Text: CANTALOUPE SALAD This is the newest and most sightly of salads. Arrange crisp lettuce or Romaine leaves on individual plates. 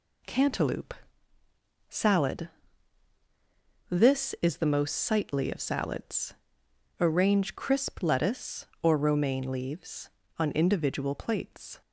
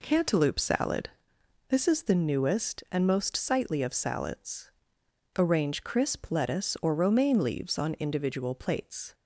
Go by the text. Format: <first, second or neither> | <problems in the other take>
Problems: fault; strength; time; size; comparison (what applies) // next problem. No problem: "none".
second | pauses between "CANTALOUPE" and "SALAD"; noticeable; at 0.9 s; 0.94 s long // pauses between "SALAD" and "This"; strong; at 2.4 s; 1.4 s long; noticeable in the second // skips "newest and"; at 4.6 s